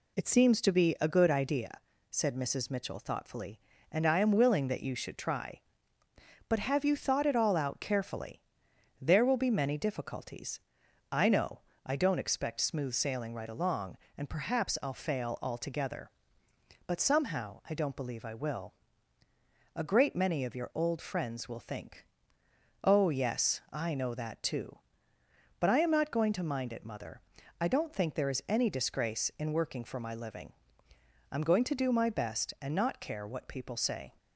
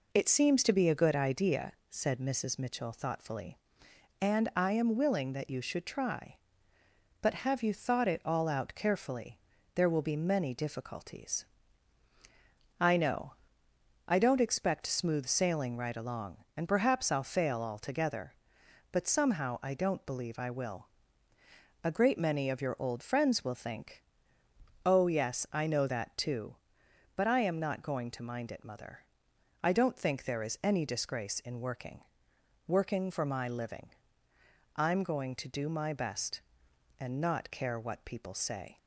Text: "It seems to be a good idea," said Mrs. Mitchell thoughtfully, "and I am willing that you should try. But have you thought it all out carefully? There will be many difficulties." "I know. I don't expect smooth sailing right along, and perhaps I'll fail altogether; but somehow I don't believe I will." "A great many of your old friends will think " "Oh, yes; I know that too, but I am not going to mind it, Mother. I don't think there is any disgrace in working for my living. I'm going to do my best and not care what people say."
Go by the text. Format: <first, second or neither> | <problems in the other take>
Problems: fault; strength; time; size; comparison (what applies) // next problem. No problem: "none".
first | says "working" twice; at 32.6 s